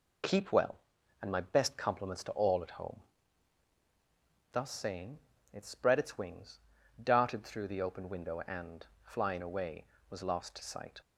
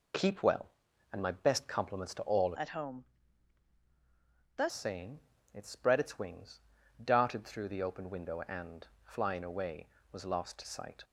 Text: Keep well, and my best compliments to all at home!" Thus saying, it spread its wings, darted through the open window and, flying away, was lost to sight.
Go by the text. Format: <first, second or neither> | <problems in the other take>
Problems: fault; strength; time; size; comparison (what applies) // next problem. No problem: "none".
first | changes voice from "at" to "Thus"; from 2.5 to 4.6 s; 2.1 s long